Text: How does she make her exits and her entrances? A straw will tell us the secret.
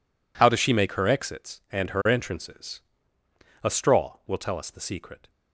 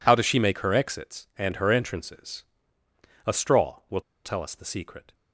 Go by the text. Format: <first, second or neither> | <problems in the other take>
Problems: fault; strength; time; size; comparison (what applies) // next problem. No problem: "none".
first | pauses between "will" and "tell"; slight; at 4.0 s; 0.24 s long